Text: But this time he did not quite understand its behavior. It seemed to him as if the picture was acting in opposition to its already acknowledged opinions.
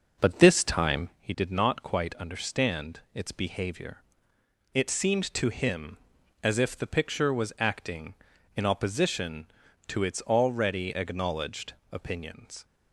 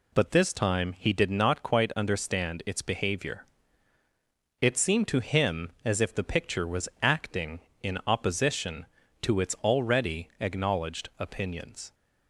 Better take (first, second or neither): second